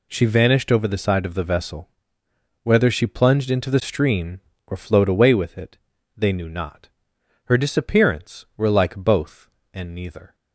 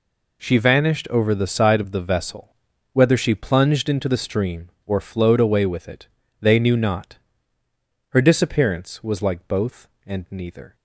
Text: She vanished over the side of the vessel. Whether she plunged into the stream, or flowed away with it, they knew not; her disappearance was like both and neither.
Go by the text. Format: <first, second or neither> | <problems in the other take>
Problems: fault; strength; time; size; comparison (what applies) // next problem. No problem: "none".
second | says "were" for "was"; at 8.5 s